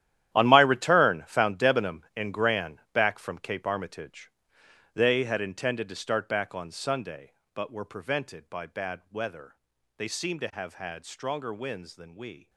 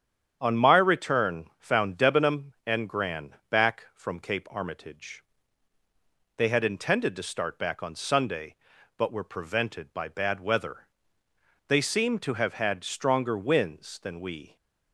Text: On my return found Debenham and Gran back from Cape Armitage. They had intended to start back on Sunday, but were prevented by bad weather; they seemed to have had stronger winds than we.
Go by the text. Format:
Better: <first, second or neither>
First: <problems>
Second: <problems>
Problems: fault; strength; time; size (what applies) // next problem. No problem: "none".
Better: second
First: gets quieter; strong; throughout; 14 dB // starts louder than the rest; strong; until 1.3 s; 11.5 dB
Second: starts louder than the rest; strong; until 1.4 s; 8.5 dB